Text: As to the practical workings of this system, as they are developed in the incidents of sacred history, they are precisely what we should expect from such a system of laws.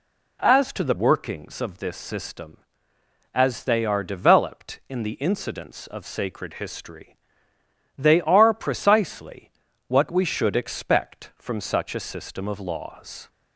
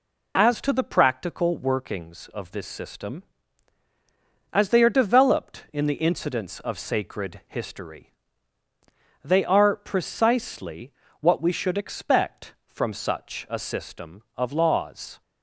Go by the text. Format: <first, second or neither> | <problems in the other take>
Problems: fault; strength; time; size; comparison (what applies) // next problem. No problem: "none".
second | skips "practical"; at 0.9 s // pauses between "precisely" and "what"; slight; at 9.5 s; 0.36 s long; slight in the second